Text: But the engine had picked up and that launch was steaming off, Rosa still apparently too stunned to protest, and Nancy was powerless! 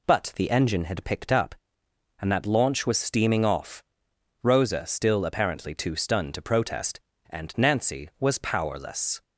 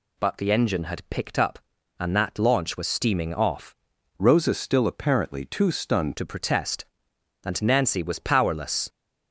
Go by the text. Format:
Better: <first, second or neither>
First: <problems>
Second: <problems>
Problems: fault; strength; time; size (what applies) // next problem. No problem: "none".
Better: first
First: none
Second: changes voice from "Rosa" to "stunned"; from 4.1 to 6.1 s; 2.0 s long